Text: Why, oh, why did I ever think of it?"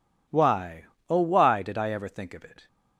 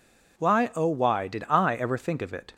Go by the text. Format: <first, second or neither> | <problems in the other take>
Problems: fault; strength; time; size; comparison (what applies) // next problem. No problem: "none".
neither | none